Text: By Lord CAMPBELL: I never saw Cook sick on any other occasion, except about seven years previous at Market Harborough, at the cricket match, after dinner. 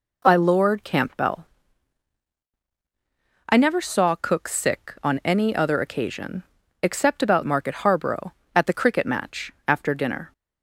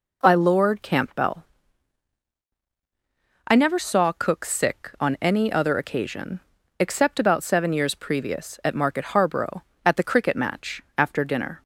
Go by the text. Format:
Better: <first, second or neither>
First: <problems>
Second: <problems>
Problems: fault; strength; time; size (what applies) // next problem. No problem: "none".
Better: second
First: skips "seven years previous at"; at 7.4 s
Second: none